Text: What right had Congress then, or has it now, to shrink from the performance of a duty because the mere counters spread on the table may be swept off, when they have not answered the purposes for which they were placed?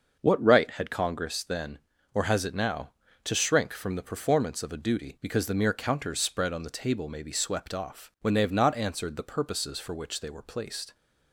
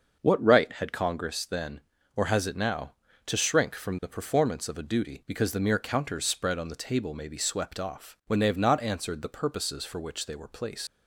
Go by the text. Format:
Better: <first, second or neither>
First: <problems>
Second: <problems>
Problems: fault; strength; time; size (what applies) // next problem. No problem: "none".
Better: first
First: starts louder than the rest; until 1.2 s; 6.5 dB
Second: starts louder than the rest; until 1.2 s; 6.5 dB // leaves "placed" unfinished; at 10.8 s; 125 ms